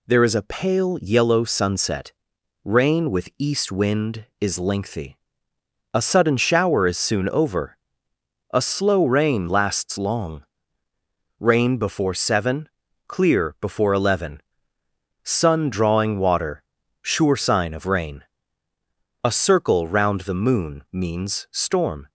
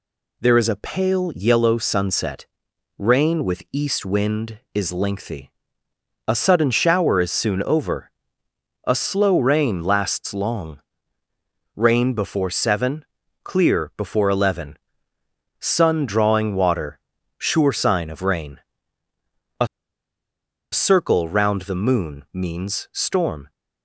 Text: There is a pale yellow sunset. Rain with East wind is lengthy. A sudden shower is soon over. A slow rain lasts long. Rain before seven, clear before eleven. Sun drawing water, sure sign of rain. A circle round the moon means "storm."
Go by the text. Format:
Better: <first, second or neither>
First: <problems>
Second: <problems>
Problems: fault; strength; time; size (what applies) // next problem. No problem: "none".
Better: first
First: none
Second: pauses between "A" and "circle"; at 19.6 s; 1.0 s long